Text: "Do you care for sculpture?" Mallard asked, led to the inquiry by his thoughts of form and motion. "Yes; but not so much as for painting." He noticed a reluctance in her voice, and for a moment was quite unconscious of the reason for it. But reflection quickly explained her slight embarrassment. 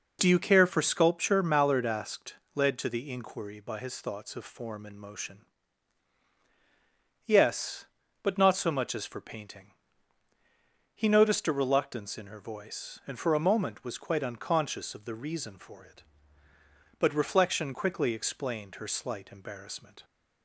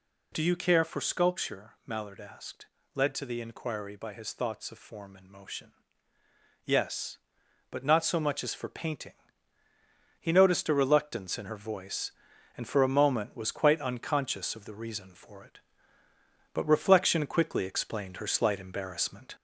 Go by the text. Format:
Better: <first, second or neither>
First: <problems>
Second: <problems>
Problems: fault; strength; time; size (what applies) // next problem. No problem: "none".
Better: first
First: none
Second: gets louder; slight; throughout; 2 dB